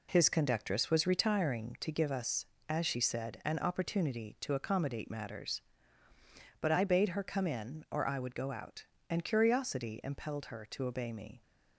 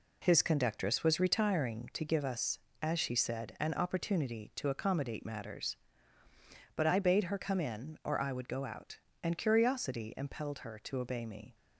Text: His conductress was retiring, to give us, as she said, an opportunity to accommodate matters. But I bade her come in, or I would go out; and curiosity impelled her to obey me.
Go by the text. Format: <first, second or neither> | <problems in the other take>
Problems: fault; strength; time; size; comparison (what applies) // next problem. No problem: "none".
neither | none